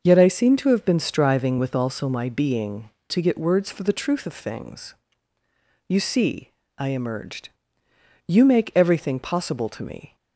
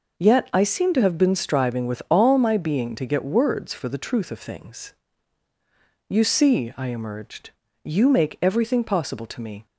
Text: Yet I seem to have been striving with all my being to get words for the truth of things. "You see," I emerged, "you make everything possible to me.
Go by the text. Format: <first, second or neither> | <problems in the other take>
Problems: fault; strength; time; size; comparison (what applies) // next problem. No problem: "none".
second | starts louder than the rest; noticeable; until 1.0 s; 6 dB // says "also" for "all"; at 1.7 s